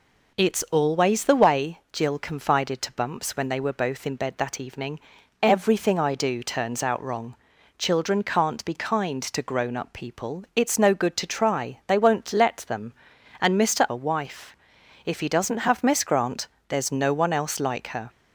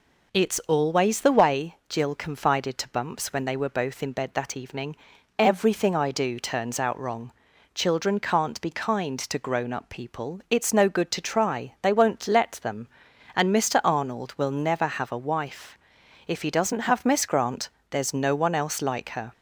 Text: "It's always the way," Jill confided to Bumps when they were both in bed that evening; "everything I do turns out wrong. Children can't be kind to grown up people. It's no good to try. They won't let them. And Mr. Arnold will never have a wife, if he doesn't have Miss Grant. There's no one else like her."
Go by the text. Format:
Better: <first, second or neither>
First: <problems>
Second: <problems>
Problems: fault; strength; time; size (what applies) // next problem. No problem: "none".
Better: second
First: skips "Arnold will never have"; at 13.8 s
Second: none